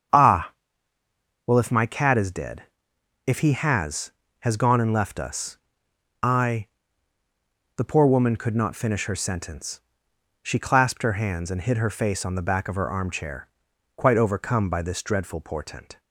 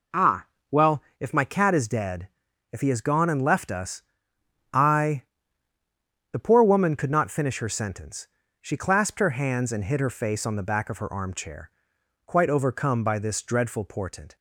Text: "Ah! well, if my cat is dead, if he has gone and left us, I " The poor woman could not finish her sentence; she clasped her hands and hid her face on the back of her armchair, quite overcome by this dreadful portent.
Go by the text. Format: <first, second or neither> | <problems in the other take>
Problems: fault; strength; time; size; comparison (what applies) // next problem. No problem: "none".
second | starts louder than the rest; strong; until 2.0 s; 7.5 dB // says "has" twice; at 4.3 s